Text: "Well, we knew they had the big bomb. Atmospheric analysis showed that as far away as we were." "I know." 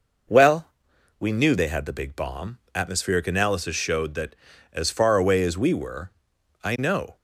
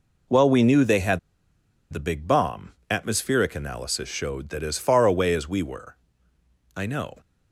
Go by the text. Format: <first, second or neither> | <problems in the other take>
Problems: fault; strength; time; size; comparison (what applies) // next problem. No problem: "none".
first | pauses between "had" and "the"; noticeable; at 1.1 s; 0.71 s long